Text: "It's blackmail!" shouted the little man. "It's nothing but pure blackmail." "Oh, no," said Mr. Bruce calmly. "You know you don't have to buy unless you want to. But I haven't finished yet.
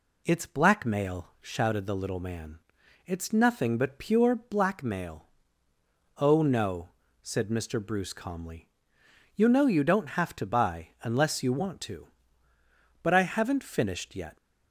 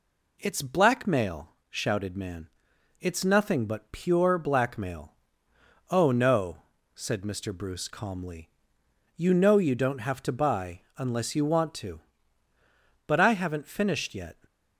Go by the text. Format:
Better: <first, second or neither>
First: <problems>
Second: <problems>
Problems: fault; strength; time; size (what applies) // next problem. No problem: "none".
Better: first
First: none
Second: skips "the little"; at 2.1 s